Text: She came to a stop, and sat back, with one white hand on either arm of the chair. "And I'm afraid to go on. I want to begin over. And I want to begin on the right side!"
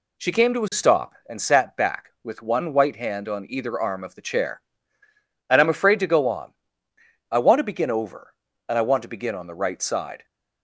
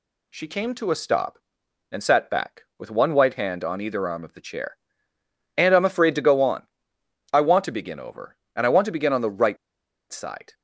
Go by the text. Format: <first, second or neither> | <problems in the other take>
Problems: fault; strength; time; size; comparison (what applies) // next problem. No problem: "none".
first | pauses between "right" and "side"; noticeable; at 9.5 s; 0.54 s long